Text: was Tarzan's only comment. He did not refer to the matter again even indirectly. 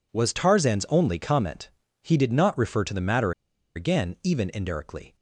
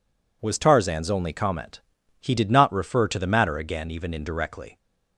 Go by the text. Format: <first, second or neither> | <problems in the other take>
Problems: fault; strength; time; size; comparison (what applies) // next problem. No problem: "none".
second | pauses between "matter" and "again"; at 3.3 s; 0.44 s long